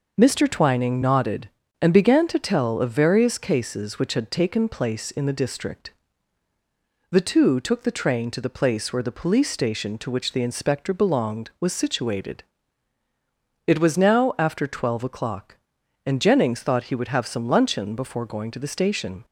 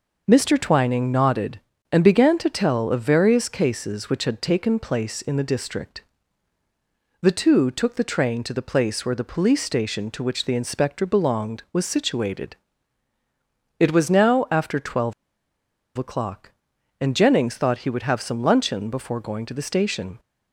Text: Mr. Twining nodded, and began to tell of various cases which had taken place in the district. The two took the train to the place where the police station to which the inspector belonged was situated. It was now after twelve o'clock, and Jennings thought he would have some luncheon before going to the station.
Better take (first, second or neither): first